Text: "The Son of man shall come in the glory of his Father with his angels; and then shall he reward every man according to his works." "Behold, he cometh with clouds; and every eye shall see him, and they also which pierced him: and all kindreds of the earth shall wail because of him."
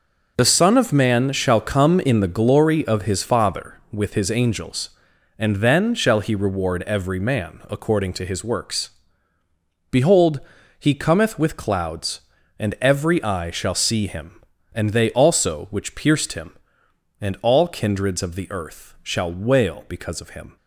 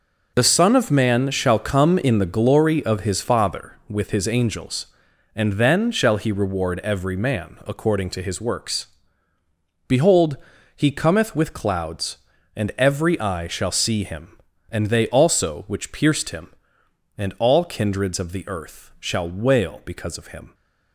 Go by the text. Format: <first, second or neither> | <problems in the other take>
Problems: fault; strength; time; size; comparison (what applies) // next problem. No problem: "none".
neither | none